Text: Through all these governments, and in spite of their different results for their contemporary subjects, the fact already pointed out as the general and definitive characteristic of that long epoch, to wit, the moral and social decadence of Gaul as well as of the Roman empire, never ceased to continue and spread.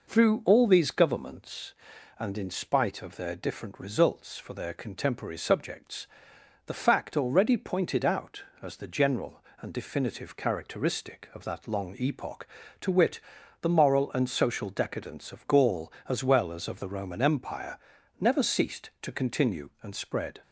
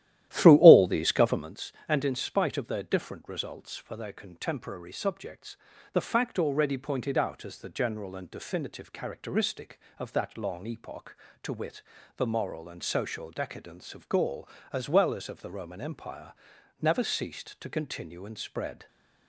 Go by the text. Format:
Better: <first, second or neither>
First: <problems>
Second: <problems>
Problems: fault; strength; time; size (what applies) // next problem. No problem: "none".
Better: first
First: none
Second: starts louder than the rest; strong; until 1.5 s; 13 dB